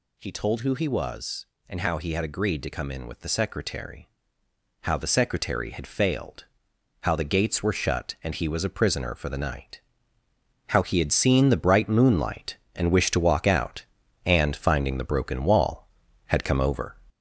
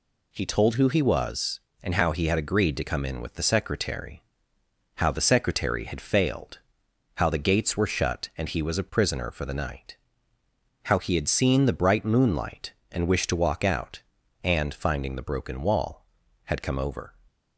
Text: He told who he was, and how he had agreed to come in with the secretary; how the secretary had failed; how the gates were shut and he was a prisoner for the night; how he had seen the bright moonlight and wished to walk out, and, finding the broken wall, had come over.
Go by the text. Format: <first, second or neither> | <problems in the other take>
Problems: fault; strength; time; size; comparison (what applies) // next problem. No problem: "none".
second | gets louder; noticeable; throughout; 5 dB